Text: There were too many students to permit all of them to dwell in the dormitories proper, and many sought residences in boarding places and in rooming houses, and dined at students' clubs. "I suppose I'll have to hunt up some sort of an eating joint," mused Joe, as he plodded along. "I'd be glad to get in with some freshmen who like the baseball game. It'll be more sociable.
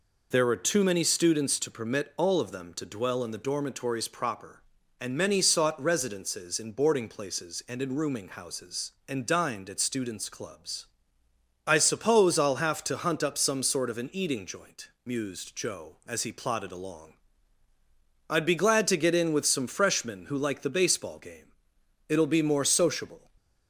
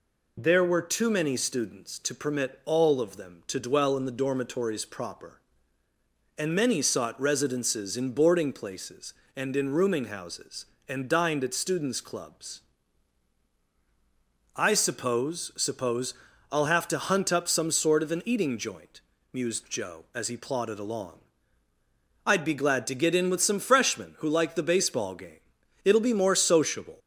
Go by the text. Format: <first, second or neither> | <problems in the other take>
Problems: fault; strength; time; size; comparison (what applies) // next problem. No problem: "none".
first | says "suppose" twice; at 15.5 s